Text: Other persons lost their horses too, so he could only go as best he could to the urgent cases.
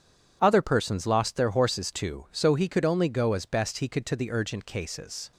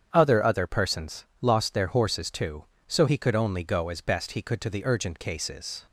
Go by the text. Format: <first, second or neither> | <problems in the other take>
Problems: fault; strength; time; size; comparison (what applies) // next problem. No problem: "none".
first | starts louder than the rest; strong; until 1.1 s; 8 dB // says "Other" twice; at 0.4 s // pauses between "persons" and "lost"; slight; at 1.2 s; 0.16 s long